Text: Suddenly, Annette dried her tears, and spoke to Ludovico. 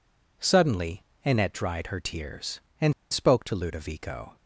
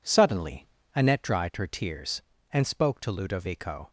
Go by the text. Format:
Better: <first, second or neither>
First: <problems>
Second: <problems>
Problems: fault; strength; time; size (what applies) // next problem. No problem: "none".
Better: second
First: pauses between "and" and "spoke"; slight; at 2.9 s; 0.19 s long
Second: none